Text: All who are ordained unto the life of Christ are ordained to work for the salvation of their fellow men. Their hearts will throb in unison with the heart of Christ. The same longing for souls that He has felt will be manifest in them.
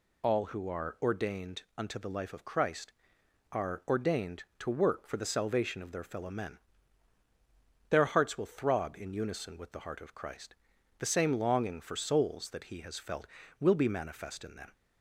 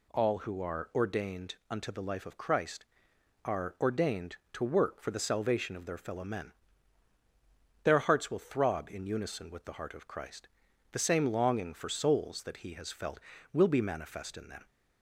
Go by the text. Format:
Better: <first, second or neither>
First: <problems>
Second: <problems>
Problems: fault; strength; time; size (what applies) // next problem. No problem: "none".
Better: second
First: loses the start of "All"; at 0.2 s; 60 ms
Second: none